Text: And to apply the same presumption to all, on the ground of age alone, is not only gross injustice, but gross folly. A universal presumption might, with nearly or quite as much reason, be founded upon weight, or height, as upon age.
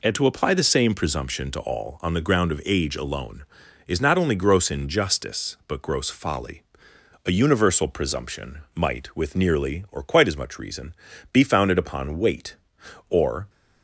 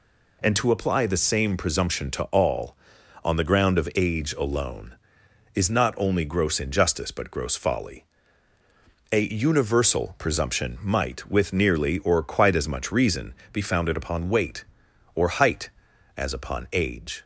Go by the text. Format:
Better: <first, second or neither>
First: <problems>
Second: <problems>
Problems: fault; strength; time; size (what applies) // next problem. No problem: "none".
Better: second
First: stops before "height as upon age"; at 13.4 s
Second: none